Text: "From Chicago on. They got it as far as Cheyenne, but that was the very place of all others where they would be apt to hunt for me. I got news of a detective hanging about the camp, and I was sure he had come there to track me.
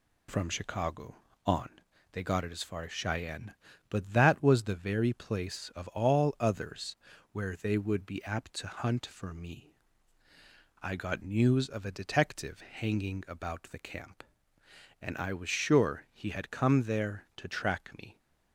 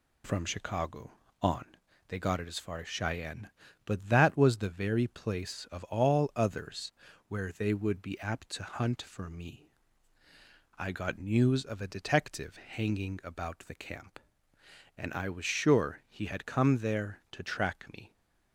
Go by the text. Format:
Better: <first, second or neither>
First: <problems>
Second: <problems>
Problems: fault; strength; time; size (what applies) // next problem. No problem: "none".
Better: neither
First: pauses between "others" and "where"; slight; at 6.9 s; 0.34 s long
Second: pauses between "others" and "where"; slight; at 6.9 s; 0.34 s long